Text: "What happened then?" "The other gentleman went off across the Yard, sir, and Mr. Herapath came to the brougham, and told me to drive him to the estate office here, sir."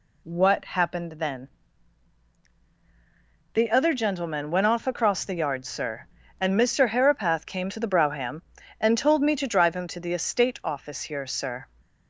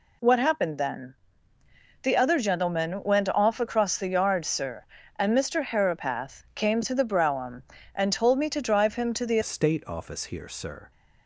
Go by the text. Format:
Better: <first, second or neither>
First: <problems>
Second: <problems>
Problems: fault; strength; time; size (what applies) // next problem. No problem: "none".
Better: first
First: none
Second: changes voice at "estate"; from 9.4 s on; 1.5 s long